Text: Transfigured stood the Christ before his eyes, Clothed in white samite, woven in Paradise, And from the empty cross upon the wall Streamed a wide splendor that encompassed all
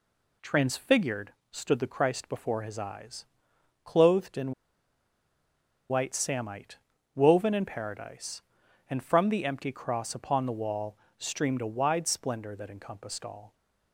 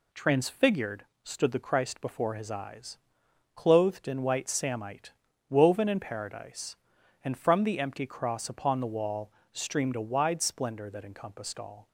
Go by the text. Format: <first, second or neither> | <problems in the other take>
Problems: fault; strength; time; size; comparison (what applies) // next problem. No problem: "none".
second | pauses between "Transfigured" and "stood"; slight; at 1.3 s; 0.20 s long; slight in the second // pauses between "in" and "white"; strong; at 4.5 s; 1.3 s long // pauses between "wall" and "Streamed"; slight; at 10.9 s; 0.20 s long; slight in the second